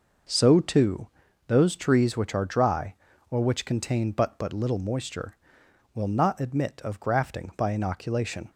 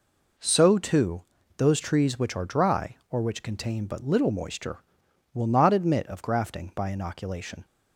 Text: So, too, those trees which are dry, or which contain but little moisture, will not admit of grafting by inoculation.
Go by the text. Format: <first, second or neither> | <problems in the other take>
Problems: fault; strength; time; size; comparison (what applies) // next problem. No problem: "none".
second | says "but" twice; at 4.3 s